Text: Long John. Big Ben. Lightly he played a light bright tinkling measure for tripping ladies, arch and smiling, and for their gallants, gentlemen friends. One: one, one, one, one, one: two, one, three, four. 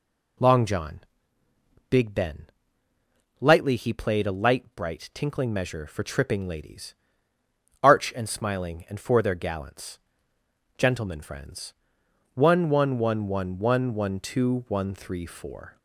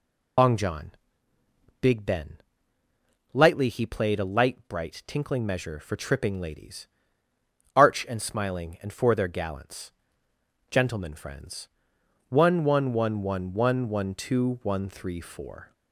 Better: first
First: none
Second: loses the start of "Long"; at 0.3 s; 70 ms

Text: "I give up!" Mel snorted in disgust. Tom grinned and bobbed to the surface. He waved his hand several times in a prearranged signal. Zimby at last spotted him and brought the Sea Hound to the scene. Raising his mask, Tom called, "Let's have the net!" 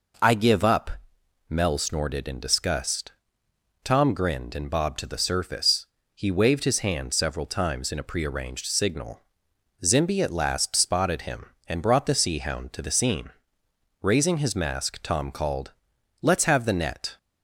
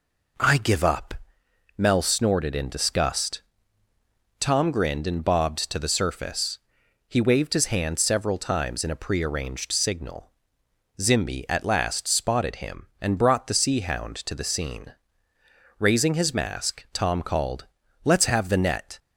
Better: neither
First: none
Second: none

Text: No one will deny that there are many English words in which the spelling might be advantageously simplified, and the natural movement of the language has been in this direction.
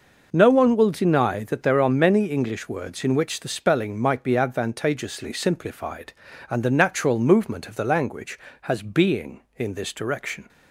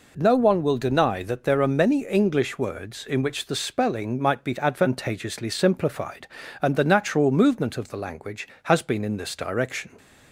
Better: second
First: says "being" for "been"; at 8.8 s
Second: none

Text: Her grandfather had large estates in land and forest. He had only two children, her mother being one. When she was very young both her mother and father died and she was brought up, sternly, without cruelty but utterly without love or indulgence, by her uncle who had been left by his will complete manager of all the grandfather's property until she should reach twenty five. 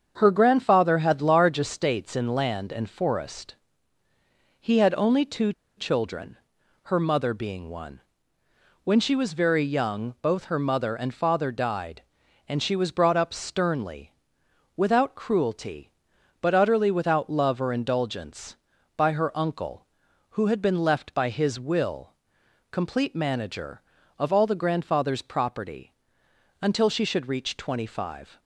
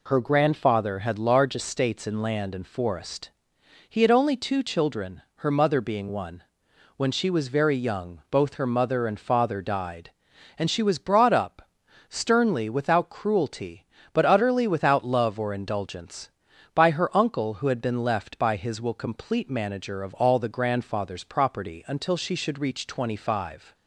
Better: second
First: starts louder than the rest; strong; until 1.1 s; 7 dB // pauses between "two" and "children"; slight; at 5.5 s; 0.24 s long // pauses between "will" and "complete"; noticeable; at 22.1 s; 0.60 s long // pauses between "property" and "until"; noticeable; at 25.9 s; 0.70 s long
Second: none

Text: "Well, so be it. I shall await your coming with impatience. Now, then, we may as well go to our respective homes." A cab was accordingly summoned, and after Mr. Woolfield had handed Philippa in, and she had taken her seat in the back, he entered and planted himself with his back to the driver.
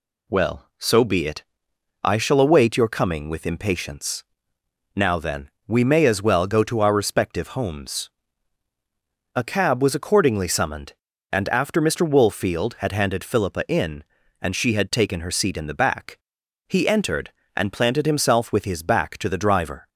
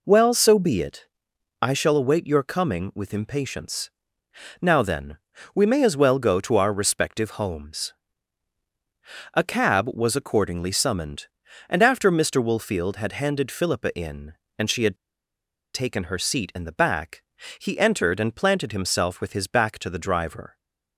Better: first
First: none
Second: pauses between "had" and "taken"; noticeable; at 14.9 s; 0.79 s long

